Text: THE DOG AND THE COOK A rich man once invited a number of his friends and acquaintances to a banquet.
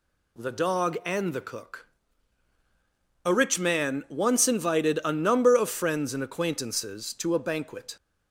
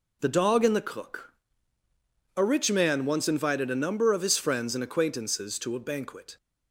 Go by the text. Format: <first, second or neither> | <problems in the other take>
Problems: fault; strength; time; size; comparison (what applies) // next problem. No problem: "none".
second | pauses between "COOK" and "A"; strong; at 1.8 s; 1.3 s long; also in the second // skips "his"; at 5.6 s